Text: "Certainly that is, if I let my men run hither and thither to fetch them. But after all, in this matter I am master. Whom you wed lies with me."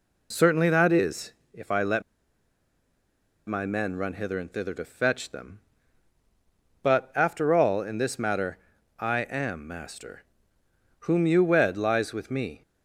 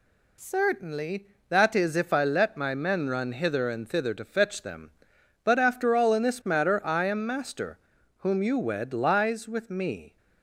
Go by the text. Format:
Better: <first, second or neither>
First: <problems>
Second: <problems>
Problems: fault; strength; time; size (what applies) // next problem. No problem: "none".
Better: second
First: pauses between "let" and "my"; strong; at 2.0 s; 1.4 s long // pauses between "matter" and "I"; at 8.5 s; 0.42 s long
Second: none